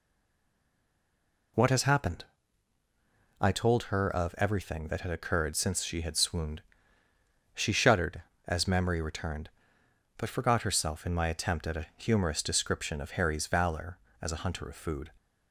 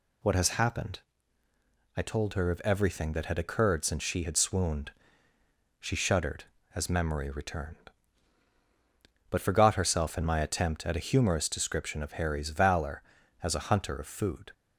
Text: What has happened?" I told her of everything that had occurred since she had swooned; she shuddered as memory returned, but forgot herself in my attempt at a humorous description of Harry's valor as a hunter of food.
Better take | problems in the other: second | stays silent before the first word; noticeable; until 1.5 s; 1.5 s long

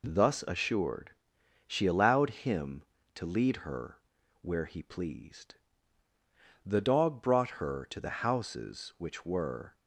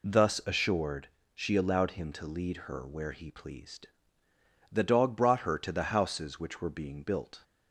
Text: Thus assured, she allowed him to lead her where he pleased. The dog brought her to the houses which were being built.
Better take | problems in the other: second | pauses between "her" and "where"; noticeable; at 3.9 s; 0.46 s long // stops before "being built"; at 9.7 s

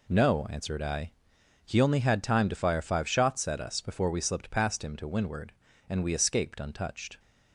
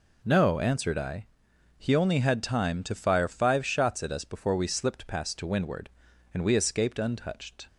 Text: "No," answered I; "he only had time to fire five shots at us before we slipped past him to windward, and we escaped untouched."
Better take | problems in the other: first | skips "him"; at 5.3 s

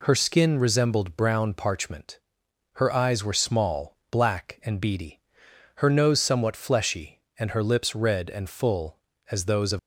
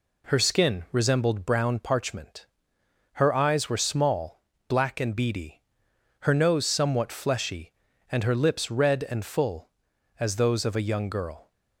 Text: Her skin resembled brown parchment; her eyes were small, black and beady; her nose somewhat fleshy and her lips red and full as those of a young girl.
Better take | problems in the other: second | stops before "a young girl"; at 9.7 s

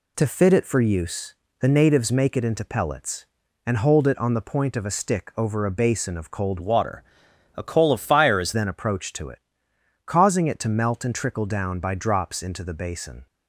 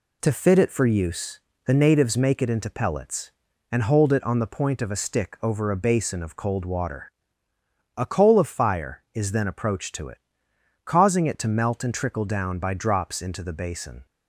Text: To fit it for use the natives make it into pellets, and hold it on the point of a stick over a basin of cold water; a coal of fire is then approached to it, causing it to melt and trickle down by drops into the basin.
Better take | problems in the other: second | pauses between "use" and "the"; slight; at 1.3 s; 0.26 s long; slight in the second // changes voice from "water" to "is"; from 6.6 to 8.5 s; 1.9 s long

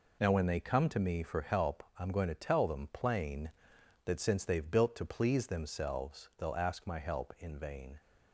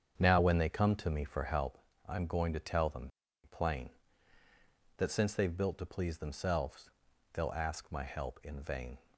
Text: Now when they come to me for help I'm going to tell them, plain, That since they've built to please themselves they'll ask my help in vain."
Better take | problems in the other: first | starts louder than the rest; strong; until 1.7 s; 7.5 dB // pauses between "help" and "I'm"; slight; at 1.7 s; 0.30 s long; slight in the first // pauses between "themselves" and "they'll"; at 6.8 s; 0.44 s long

